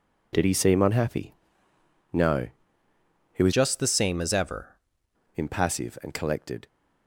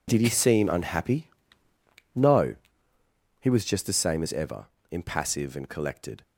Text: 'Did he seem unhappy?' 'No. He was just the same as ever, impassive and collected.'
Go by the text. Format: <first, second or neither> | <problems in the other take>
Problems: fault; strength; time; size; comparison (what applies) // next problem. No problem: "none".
second | changes voice from "just" to "ever"; from 3.5 to 4.7 s; 1.2 s long